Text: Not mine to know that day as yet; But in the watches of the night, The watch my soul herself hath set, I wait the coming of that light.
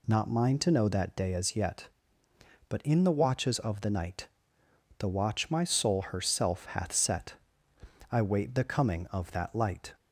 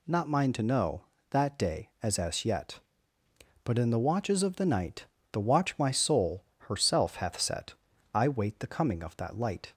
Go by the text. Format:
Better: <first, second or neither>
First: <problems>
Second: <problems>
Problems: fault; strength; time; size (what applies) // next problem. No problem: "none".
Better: first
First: none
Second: says "as" twice; at 2.1 s // pauses between "soul" and "herself"; slight; at 6.4 s; 0.26 s long